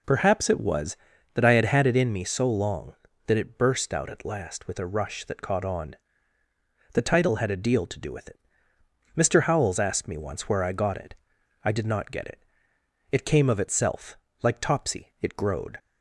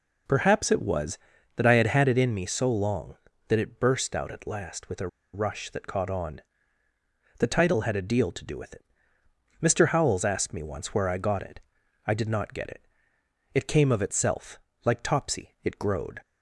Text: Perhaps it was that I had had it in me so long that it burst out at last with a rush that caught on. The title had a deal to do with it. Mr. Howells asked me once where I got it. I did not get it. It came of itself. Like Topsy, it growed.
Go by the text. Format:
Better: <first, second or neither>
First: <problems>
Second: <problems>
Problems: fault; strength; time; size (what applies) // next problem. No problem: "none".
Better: first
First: none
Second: pauses between "a" and "rush"; slight; at 5.0 s; 0.26 s long